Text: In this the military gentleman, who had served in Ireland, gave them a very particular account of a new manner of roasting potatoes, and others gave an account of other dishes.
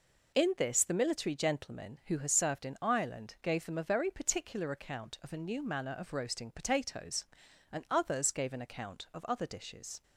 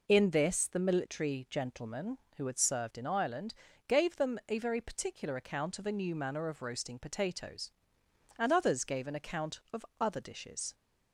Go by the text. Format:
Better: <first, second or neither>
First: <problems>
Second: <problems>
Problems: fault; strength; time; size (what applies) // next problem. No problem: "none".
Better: second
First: says "has" for "had"; at 2.1 s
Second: none